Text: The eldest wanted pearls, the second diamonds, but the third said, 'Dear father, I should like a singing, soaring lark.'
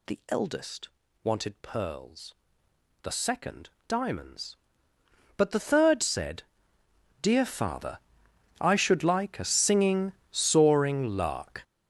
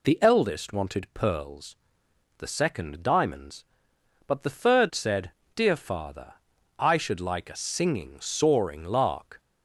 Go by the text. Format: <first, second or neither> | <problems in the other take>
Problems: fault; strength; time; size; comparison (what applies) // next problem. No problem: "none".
second | gets louder; strong; throughout; 13 dB // pauses between "eldest" and "wanted"; slight; at 0.8 s; 0.34 s long // pauses between "second" and "diamonds"; slight; at 3.6 s; 0.18 s long